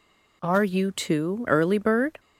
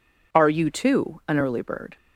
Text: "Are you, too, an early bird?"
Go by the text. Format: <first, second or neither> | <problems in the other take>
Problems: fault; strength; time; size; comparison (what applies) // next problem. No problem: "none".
second | skips "an"; at 1.4 s